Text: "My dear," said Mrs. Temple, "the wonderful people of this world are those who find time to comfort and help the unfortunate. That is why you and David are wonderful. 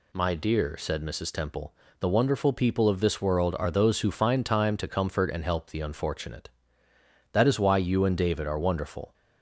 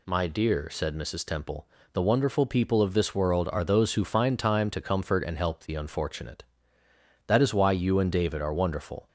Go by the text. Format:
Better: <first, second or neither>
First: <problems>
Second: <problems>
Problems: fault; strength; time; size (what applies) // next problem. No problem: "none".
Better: neither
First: none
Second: none